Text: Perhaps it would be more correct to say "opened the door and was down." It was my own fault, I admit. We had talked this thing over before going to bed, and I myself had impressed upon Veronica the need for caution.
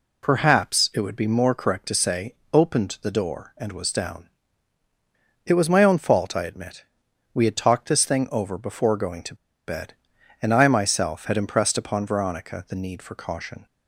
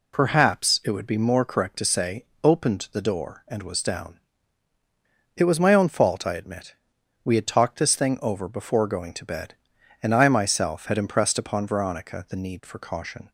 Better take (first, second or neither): second